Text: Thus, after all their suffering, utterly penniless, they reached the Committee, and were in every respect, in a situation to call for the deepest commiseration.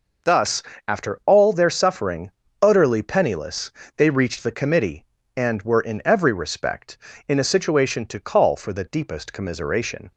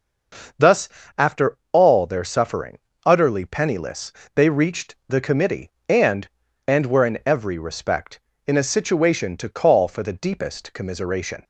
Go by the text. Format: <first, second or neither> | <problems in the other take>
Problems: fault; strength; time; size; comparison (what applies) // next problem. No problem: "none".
first | starts louder than the rest; until 2.0 s; 6 dB // pauses between "after" and "all"; slight; at 1.5 s; 0.16 s long // says "and" twice; at 6.6 s